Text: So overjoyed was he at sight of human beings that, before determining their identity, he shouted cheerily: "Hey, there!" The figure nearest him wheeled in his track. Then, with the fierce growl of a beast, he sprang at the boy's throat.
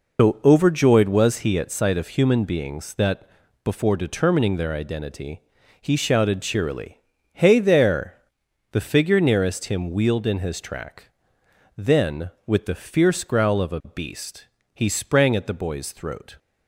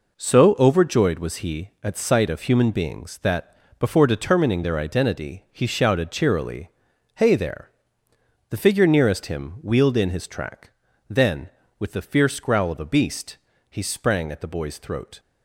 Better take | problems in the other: second | loses the start of "So"; at 0.1 s; 135 ms

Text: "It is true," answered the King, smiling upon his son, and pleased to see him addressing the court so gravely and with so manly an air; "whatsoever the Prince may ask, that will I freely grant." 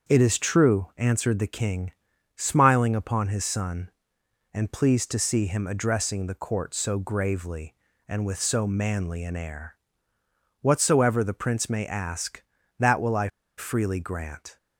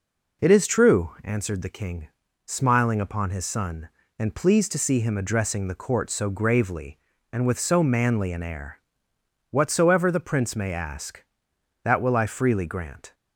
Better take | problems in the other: second | starts louder than the rest; until 1.1 s; 6.5 dB // pauses between "I" and "freely"; slight; at 13.2 s; 0.30 s long

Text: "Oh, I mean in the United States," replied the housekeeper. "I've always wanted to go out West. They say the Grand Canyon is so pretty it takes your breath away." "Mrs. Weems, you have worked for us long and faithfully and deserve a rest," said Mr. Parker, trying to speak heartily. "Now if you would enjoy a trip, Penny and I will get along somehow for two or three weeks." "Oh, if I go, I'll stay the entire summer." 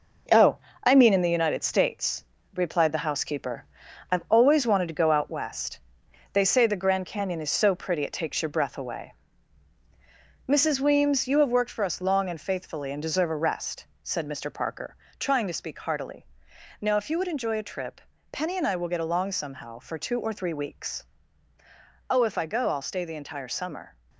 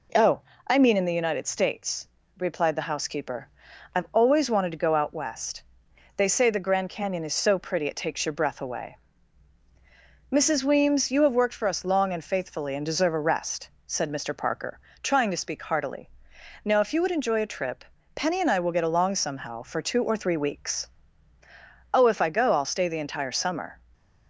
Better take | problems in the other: second | gets quieter; throughout; 6.5 dB

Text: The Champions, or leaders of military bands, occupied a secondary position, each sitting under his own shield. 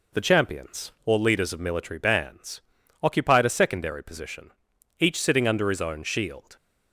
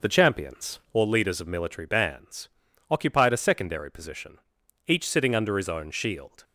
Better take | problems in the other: first | starts louder than the rest; noticeable; until 1.1 s; 5.5 dB

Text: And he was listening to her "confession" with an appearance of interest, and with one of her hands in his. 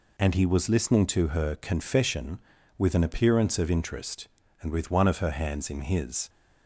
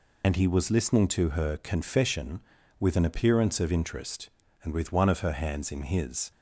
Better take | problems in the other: first | loses the start of "And"; at 0.2 s; 45 ms

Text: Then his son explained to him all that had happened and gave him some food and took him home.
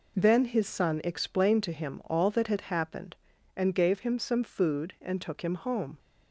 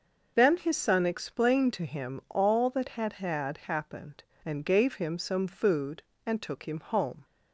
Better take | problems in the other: first | starts louder than the rest; until 1.3 s; 6 dB // says "had" twice; at 3.1 s

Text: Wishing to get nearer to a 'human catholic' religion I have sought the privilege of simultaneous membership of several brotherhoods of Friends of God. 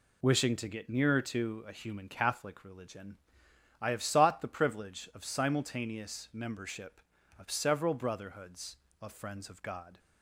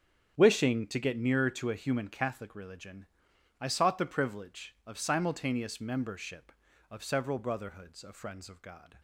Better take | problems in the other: first | starts louder than the rest; strong; until 1.3 s; 8.5 dB // pauses between "religion" and "I"; noticeable; at 3.0 s; 0.54 s long; noticeable in the first // skips "have"; at 3.6 s

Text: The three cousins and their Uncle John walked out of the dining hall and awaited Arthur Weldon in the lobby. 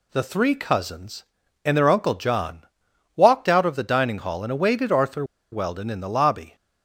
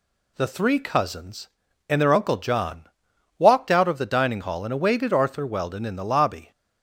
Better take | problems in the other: second | pauses between "John" and "walked"; noticeable; at 2.6 s; 0.52 s long; noticeable in the second // pauses between "Arthur" and "Weldon"; slight; at 5.2 s; 0.28 s long

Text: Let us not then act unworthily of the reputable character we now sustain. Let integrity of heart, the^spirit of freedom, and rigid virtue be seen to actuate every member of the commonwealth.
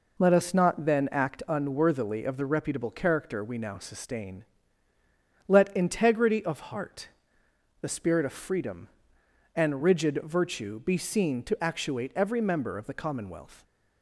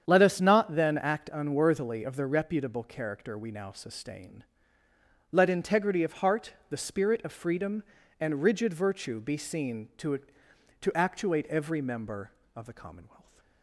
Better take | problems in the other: first | starts louder than the rest; strong; until 1.0 s; 8 dB // says "to" twice; at 10.8 s

